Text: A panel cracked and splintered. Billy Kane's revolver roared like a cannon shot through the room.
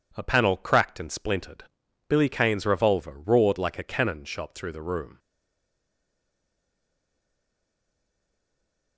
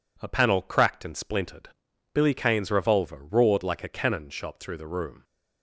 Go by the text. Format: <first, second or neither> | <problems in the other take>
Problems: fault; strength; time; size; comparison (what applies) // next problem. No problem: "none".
second | stays silent after the last word; strong; from 5.1 s on; 3.8 s long